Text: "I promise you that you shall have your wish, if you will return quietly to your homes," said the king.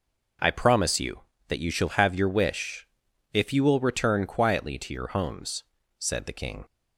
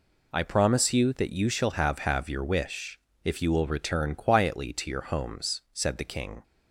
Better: first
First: none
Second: says "have" twice; at 1.9 s

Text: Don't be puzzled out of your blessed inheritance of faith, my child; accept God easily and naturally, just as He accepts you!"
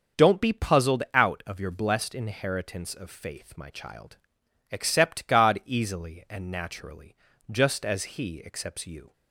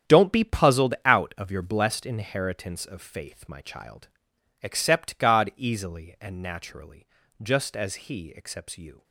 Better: first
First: starts louder than the rest; until 1.2 s; 6.5 dB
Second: gets quieter; strong; throughout; 12.5 dB // starts louder than the rest; strong; until 1.2 s; 9.5 dB

